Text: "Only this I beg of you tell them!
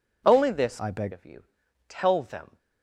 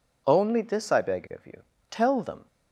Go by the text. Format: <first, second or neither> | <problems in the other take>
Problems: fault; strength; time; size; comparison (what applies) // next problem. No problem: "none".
second | changes voice from "I" to "beg"; from 0.7 to 1.1 s; 0.4 s long // pauses between "you" and "tell"; at 1.4 s; 0.44 s long; slight in the second